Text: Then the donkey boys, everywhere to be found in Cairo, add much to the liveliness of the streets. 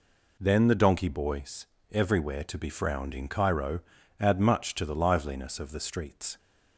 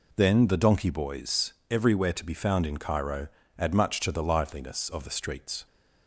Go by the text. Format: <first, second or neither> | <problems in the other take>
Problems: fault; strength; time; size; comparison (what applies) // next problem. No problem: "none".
second | says "frowned" for "found"; at 2.6 s